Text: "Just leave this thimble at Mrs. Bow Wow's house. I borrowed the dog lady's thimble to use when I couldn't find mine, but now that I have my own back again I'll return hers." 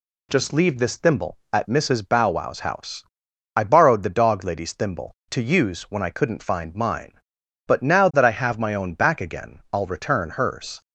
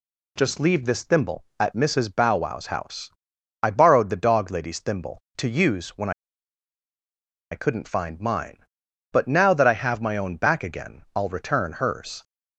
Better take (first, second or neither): first